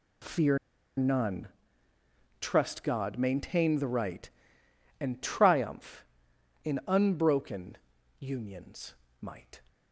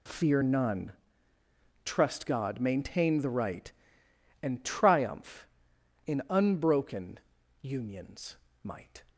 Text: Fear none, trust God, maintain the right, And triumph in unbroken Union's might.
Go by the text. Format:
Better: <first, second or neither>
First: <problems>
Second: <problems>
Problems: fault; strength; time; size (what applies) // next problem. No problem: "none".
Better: second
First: pauses between "Fear" and "none"; at 0.5 s; 0.40 s long // pauses between "unbroken" and "Union's"; at 7.7 s; 0.42 s long // pauses between "Union's" and "might"; slight; at 8.9 s; 0.26 s long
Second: pauses between "unbroken" and "Union's"; at 7.2 s; 0.42 s long // pauses between "Union's" and "might"; slight; at 8.3 s; 0.26 s long